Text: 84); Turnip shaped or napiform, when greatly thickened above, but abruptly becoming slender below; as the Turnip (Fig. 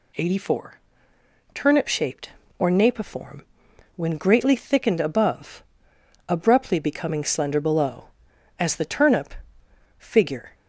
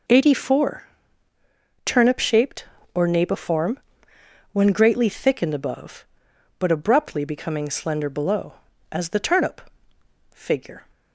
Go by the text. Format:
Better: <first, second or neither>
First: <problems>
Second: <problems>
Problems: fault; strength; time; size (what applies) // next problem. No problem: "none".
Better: second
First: skips "but"; at 5.9 s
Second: none